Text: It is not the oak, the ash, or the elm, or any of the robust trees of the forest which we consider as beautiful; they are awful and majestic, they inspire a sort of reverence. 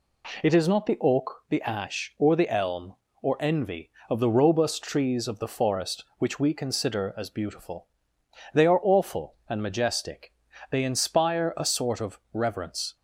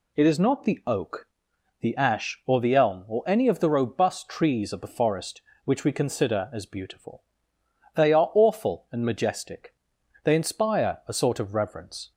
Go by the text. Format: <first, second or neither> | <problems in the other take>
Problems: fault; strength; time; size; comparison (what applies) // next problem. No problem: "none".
second | says "envy" for "any"; at 3.3 s // pauses between "of" and "reverence"; slight; at 12.1 s; 0.16 s long